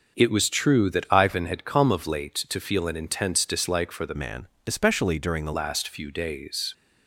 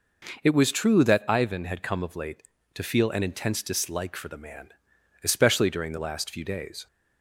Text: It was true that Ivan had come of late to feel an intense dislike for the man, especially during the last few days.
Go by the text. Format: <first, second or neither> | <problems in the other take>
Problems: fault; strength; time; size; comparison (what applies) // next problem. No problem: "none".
second | starts louder than the rest; noticeable; until 1.2 s; 6 dB // changes voice from "man" to "the"; from 4.1 to 5.5 s; 1.4 s long